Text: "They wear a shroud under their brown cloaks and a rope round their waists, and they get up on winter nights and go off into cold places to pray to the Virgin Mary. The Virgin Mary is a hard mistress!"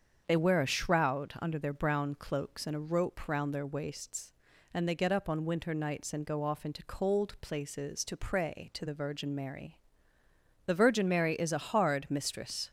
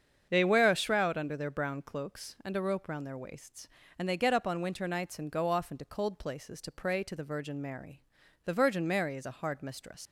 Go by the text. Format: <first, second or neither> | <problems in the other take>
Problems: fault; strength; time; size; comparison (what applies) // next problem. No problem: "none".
first | starts louder than the rest; strong; until 1.3 s; 7.5 dB; strong in the first // leaves "mistress" unfinished; at 10.0 s; 115 ms